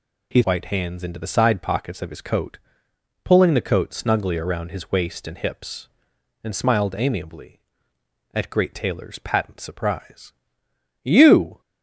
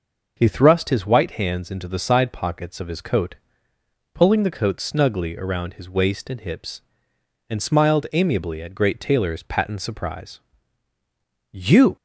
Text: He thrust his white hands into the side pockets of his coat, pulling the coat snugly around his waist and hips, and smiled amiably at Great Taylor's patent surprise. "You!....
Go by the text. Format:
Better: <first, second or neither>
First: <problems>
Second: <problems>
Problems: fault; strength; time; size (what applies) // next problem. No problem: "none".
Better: second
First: skips "thrust his"; at 0.4 s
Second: none